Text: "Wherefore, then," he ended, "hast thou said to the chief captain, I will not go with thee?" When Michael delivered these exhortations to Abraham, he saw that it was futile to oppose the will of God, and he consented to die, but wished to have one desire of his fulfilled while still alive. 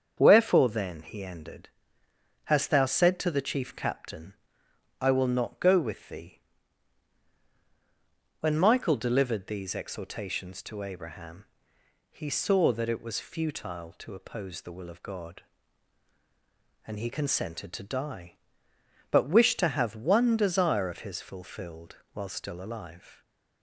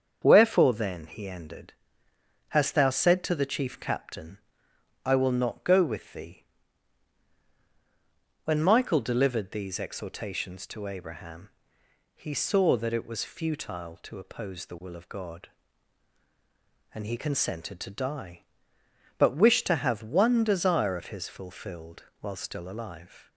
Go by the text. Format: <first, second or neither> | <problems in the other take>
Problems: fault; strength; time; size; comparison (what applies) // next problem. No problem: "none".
neither | starts louder than the rest; strong; the same in both // pauses between "fulfilled" and "while"; slight; the same in both